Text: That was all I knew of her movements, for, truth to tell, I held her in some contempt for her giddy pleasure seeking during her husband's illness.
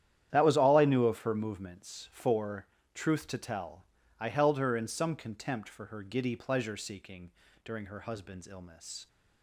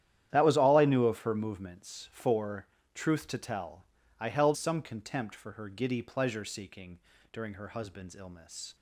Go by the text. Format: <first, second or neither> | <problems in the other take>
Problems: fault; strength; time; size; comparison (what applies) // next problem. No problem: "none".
first | starts louder than the rest; strong; until 1.3 s; 11 dB; strong in the first // skips "her in"; at 4.5 s // pauses between "seeking" and "during"; slight; at 6.9 s; 0.32 s long; slight in the first